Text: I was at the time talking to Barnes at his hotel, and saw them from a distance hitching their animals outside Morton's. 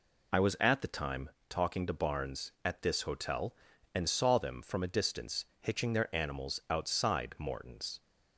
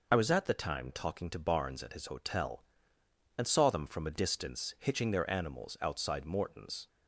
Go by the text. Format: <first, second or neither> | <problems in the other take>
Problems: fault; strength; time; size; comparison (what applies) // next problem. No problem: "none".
second | pauses between "time" and "talking"; slight; at 1.3 s; 0.18 s long // says "this" for "his"; at 2.8 s // pauses between "distance" and "hitching"; slight; at 5.4 s; 0.16 s long